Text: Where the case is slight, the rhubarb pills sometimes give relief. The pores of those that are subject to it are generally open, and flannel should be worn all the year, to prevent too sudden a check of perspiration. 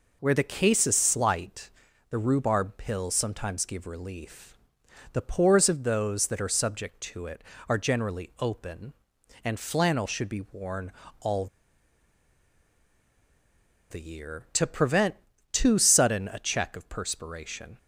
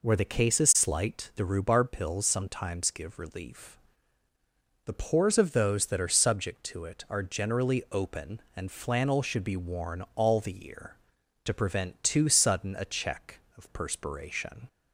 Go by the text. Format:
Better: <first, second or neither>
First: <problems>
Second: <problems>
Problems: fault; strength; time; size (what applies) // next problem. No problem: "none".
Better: second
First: pauses between "worn" and "all"; slight; at 10.9 s; 0.30 s long // pauses between "all" and "the"; strong; at 11.4 s; 2.4 s long // pauses between "prevent" and "too"; slight; at 15.1 s; 0.36 s long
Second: none